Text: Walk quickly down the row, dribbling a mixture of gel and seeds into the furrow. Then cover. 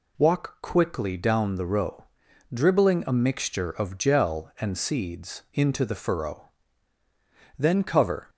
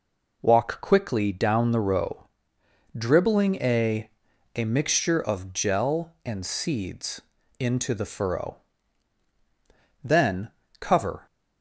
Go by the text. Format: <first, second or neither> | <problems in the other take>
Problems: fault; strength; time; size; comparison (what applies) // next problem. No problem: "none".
first | says "a" twice; at 4.5 s // pauses between "seeds" and "into"; at 7.1 s; 0.38 s long // pauses between "Then" and "cover"; slight; at 10.4 s; 0.30 s long